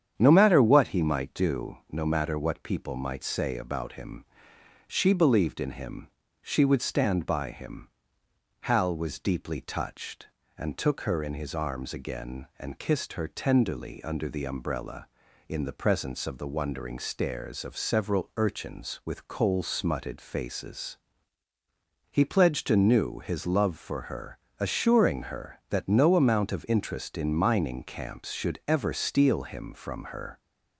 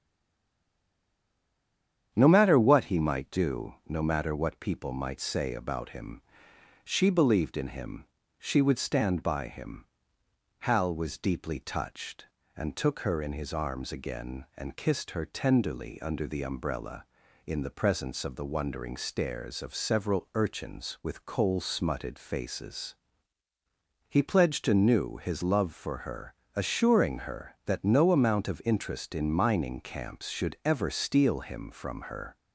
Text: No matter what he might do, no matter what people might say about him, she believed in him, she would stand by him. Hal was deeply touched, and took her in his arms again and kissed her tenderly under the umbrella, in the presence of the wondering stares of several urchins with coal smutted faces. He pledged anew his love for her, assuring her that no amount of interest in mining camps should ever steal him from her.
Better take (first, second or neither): first